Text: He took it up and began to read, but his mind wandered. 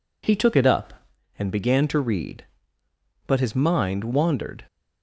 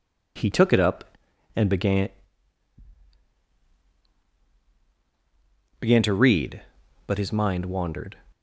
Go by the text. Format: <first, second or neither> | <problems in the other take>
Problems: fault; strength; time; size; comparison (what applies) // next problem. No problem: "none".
first | says "began" twice; at 5.8 s